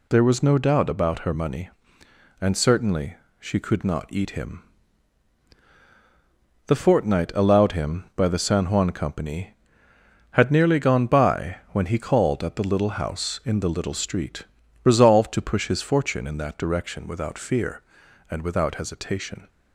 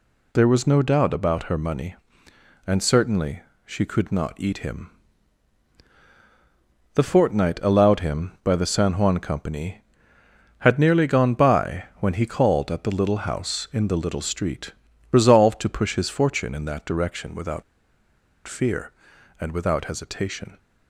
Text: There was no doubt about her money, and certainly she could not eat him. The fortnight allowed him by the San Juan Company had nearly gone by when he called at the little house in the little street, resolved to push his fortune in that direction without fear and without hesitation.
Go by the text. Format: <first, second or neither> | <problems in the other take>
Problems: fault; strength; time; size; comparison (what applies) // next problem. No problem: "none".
first | pauses between "certainly" and "she"; slight; at 3.4 s; 0.24 s long; slight in the first // pauses between "by" and "when"; slight; at 11.8 s; 0.16 s long; slight in the first // pauses between "without" and "fear"; noticeable; at 17.6 s; 0.85 s long